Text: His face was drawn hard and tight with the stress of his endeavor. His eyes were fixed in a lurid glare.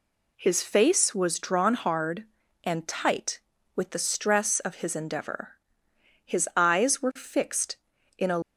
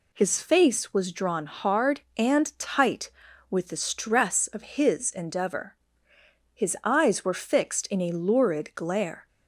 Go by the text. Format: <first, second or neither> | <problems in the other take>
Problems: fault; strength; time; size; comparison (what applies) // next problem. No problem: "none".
second | stops before "lurid glare"; at 8.4 s